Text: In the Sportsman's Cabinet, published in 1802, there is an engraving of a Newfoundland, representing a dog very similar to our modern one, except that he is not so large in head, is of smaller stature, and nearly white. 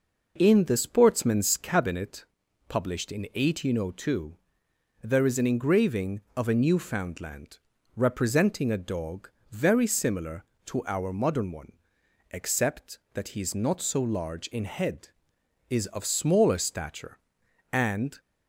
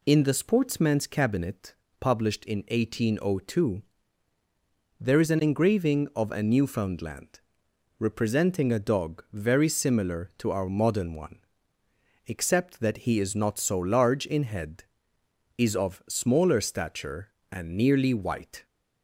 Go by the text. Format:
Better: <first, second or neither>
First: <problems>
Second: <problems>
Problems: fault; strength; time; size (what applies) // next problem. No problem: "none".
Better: second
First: pauses between "dog" and "very"; slight; at 9.2 s; 0.22 s long // stops before "nearly white"; at 18.1 s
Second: none